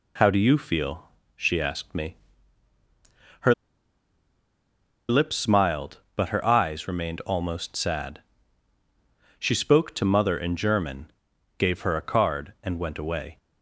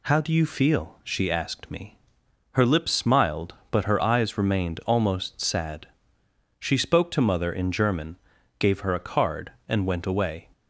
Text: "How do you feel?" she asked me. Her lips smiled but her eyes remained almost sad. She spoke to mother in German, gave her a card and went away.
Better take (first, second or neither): second